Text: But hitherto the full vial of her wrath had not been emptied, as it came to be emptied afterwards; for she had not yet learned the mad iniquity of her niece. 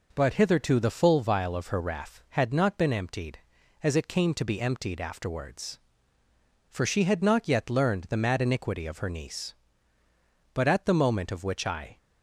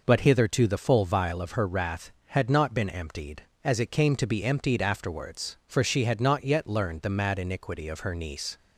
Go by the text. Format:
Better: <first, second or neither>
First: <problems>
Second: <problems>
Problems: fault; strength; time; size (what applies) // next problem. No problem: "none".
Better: second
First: goes on to say "But at the moment of which I"; from 10.5 s on; 1.4 s long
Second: none